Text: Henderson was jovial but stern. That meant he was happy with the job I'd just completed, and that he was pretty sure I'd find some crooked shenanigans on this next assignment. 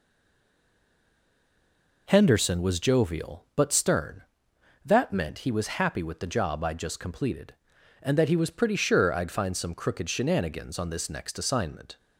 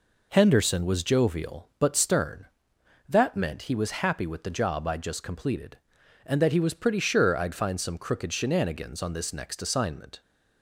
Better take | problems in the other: second | stays silent before the first word; noticeable; until 2.0 s; 2.0 s long

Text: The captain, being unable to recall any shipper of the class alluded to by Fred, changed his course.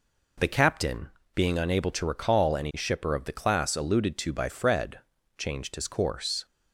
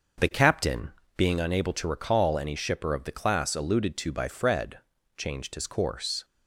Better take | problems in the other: first | starts louder than the rest; until 1.4 s; 6.5 dB

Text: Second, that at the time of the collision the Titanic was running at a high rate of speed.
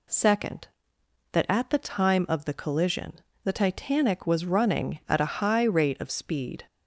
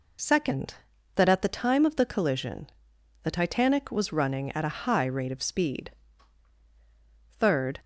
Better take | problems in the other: first | pauses between "collision" and "the"; noticeable; at 2.6 s; 0.56 s long; slight in the first // goes on to say "Third"; from 7.2 s on; 0.50 s long

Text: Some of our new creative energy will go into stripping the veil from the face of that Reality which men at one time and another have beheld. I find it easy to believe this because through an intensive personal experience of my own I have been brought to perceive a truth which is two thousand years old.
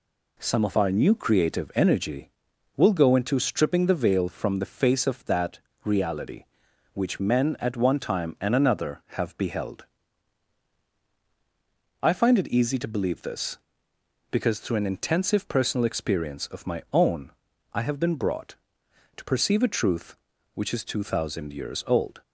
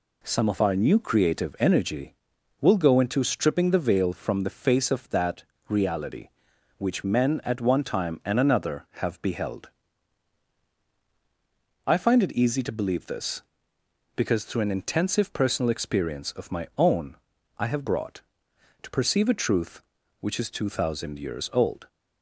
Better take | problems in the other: first | pauses between "that" and "Reality"; slight; at 5.4 s; 0.26 s long; slight in the first // pauses between "own" and "I"; at 17.1 s; 0.40 s long; also in the first // skips "been"; at 17.8 s

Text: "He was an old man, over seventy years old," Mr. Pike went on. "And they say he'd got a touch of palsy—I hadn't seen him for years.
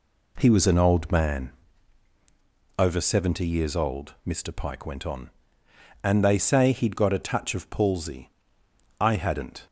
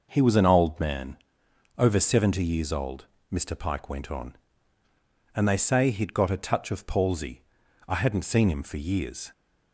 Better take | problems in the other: second | stops before "seen him for years"; at 9.6 s

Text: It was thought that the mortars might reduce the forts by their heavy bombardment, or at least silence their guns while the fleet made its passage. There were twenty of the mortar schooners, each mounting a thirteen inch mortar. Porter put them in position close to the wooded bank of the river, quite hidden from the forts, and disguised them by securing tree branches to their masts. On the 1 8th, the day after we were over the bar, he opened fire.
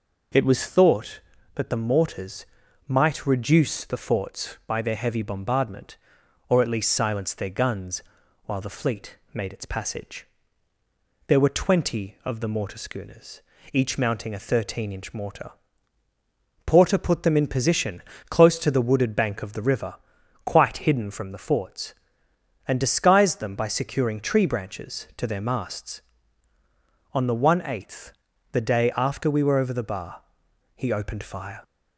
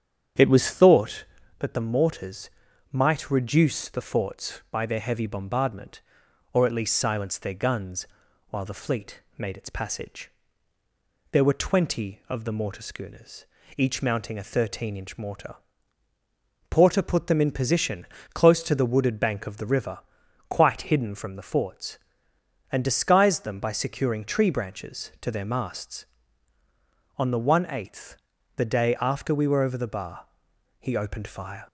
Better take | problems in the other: first | starts louder than the rest; strong; until 1.6 s; 9 dB // pauses between "mortars" and "might"; at 2.5 s; 0.40 s long; also in the first // pauses between "guns" and "while"; at 8.0 s; 0.44 s long; also in the first // pauses between "fleet" and "made"; slight; at 9.2 s; 0.16 s long; slight in the first // pauses between "position" and "close"; slight; at 18.0 s; 0.30 s long; slight in the first

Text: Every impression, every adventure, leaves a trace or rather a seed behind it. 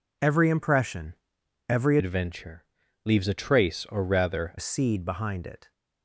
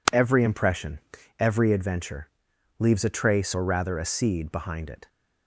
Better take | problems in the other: second | changes voice from "adventure" to "rather"; from 1.9 to 4.5 s; 2.6 s long

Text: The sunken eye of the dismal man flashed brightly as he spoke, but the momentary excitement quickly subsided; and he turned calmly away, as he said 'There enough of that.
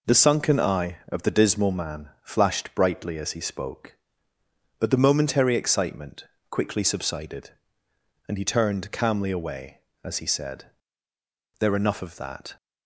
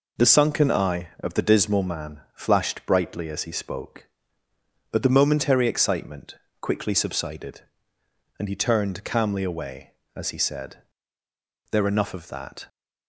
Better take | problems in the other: neither | pauses between "excitement" and "quickly"; slight; the same in both // pauses between "said" and "There"; noticeable; the same in both

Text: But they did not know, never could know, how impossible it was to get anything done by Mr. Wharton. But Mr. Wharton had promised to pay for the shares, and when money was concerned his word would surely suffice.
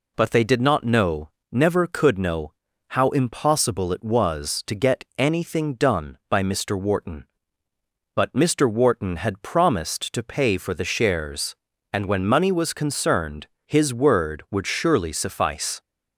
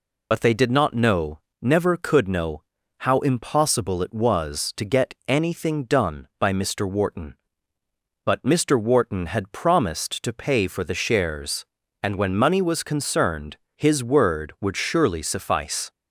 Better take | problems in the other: first | loses the start of "But"; at 0.3 s; 50 ms // pauses between "concerned" and "his"; slight; at 13.5 s; 0.18 s long; slight in the first

